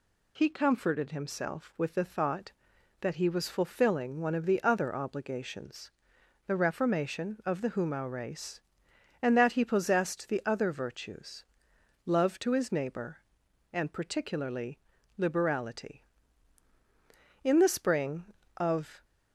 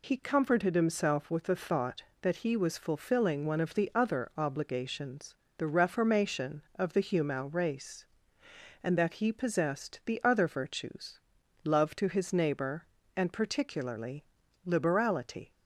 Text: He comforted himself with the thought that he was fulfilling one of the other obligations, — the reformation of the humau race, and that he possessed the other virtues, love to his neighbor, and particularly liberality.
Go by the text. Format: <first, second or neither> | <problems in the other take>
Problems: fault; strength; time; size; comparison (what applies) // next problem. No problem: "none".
second | pauses between "particularly" and "liberality"; at 14.7 s; 0.40 s long; also in the second // goes on to say "In the spring of"; from 17.4 s on; 1.6 s long